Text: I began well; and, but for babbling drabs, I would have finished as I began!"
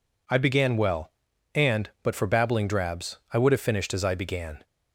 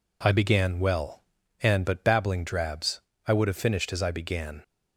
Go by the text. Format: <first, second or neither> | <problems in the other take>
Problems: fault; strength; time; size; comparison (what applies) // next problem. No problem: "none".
first | skips "for"; at 2.0 s